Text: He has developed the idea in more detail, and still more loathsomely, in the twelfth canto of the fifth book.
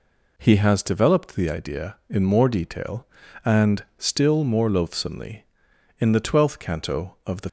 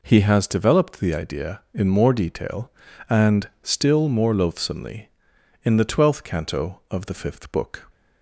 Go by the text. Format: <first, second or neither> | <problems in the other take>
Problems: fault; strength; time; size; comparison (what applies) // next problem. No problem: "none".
second | stops before "fifth book"; at 7.4 s